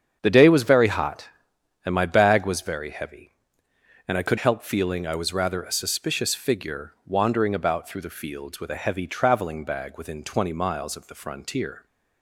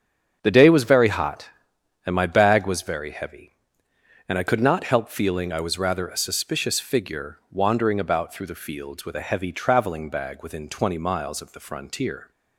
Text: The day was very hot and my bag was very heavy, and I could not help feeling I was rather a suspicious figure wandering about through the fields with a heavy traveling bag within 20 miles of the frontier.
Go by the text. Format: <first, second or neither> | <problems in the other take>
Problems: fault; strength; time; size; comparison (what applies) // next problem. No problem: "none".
second | starts louder than the rest; strong; until 1.2 s; 8 dB; strong in the second // skips "not"; at 4.3 s